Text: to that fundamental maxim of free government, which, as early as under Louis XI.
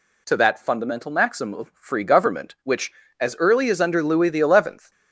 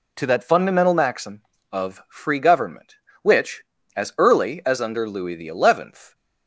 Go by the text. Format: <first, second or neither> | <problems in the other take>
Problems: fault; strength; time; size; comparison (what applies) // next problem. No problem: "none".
neither | none